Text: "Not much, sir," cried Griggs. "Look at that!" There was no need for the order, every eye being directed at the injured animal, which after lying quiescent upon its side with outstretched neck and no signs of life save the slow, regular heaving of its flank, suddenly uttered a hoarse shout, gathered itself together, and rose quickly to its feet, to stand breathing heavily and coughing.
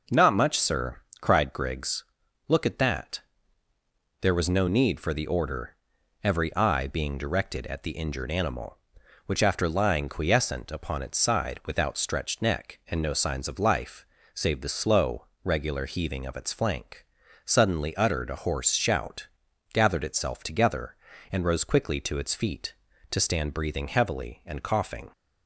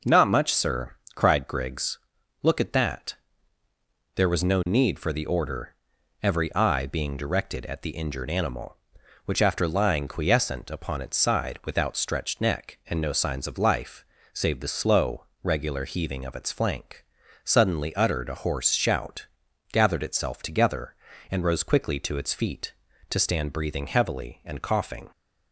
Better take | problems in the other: neither | pauses between "life" and "save"; slight; the same in both

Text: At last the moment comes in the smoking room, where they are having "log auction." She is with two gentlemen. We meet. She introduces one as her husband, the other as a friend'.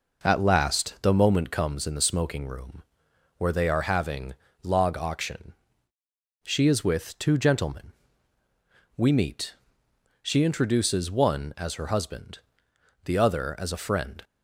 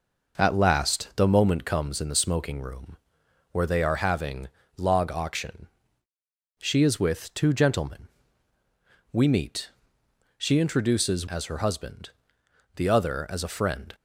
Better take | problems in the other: first | pauses between "having" and "log"; slight; at 4.4 s; 0.28 s long; slight in the first // skips "one"; at 11.2 s

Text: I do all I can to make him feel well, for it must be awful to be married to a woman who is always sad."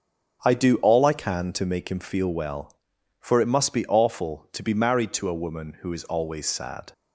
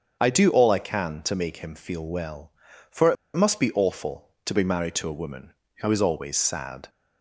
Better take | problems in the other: first | starts louder than the rest; until 1.2 s; 7 dB; noticeable in the first // pauses between "it" and "must"; slight; at 3.1 s; 0.21 s long

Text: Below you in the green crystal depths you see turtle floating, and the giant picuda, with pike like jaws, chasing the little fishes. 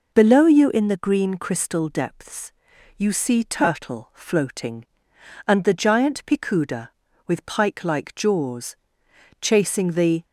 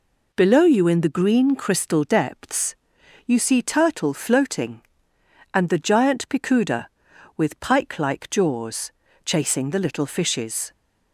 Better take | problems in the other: second | pauses between "depths" and "you"; noticeable; at 2.5 s; 0.46 s long; noticeable in the second // stops before "little fishes"; at 10.2 s

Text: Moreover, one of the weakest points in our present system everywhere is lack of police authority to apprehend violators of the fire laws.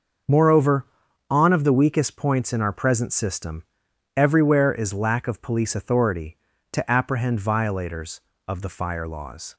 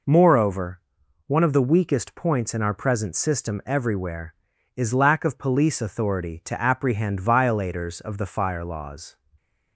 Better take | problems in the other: second | starts louder than the rest; until 1.6 s; 6 dB // says "on" for "one"; at 1.2 s // pauses between "system" and "everywhere"; noticeable; at 3.6 s; 0.54 s long

